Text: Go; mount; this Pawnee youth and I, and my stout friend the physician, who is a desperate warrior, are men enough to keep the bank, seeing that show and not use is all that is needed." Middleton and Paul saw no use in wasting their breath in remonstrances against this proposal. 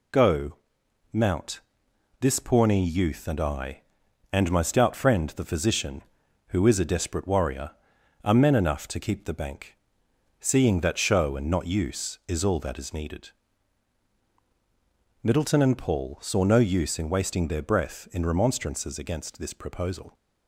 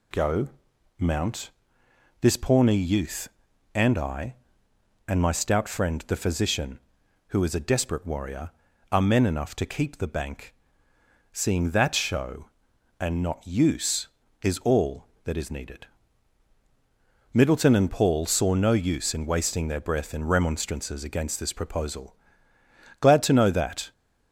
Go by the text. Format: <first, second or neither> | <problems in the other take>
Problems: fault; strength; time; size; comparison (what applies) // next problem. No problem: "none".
first | goes on to say "Glad to know that"; noticeable; from 22.9 s on; 0.92 s long